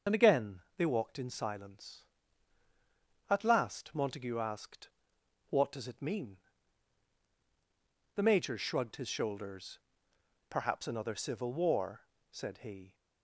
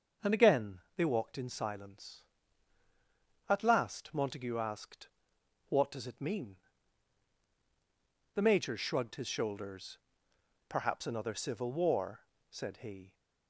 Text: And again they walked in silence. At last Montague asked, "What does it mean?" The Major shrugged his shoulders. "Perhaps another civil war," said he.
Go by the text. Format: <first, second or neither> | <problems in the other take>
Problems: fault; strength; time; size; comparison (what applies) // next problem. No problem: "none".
second | loses the start of "And"; at 0.0 s; 40 ms // starts louder than the rest; until 1.2 s; 6.5 dB; also in the second // pauses between "again" and "they"; slight; at 0.6 s; 0.16 s long; slight in the second